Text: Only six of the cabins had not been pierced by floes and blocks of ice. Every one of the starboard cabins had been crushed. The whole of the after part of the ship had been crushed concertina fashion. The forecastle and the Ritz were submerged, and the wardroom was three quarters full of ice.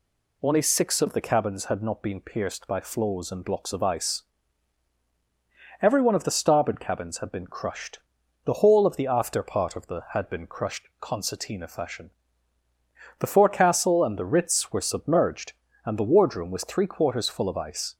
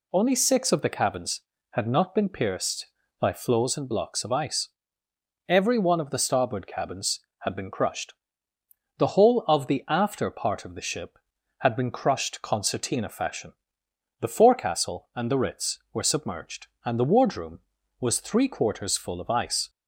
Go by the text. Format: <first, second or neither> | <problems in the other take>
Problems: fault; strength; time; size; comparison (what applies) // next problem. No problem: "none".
second | skips "ship"; at 10.0 s